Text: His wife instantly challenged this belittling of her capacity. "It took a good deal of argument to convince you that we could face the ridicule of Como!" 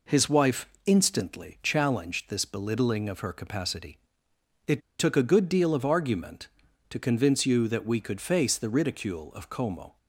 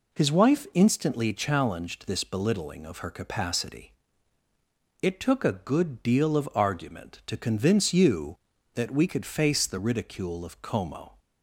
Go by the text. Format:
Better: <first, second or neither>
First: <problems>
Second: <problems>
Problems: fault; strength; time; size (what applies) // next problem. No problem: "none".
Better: second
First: pauses between "wife" and "instantly"; slight; at 0.6 s; 0.16 s long // pauses between "It" and "took"; slight; at 4.7 s; 0.20 s long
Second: none